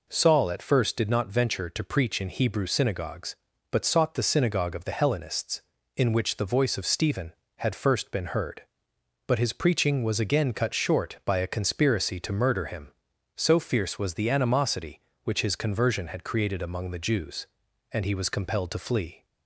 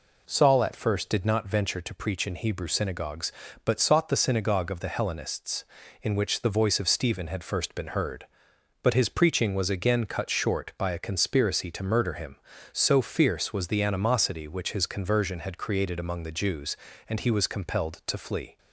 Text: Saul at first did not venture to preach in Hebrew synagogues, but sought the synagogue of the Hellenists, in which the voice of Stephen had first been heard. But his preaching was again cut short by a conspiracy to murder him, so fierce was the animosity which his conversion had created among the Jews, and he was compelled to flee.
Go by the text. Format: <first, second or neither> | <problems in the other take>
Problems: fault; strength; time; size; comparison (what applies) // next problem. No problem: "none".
neither | none